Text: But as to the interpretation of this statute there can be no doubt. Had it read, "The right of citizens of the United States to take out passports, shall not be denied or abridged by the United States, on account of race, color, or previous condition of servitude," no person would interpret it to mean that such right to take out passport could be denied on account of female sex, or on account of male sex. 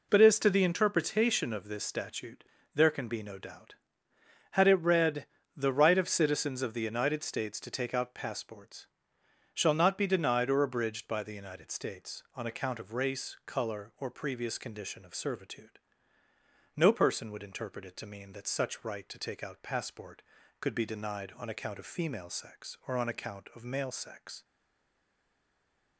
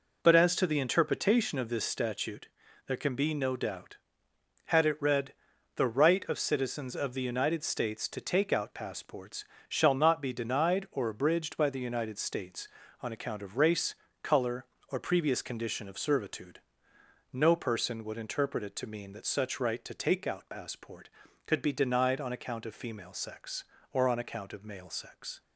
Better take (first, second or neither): second